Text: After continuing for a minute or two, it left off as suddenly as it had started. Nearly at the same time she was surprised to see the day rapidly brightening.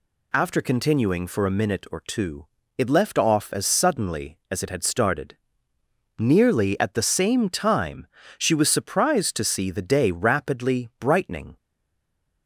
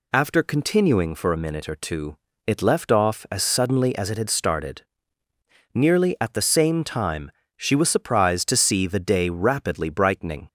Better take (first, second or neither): second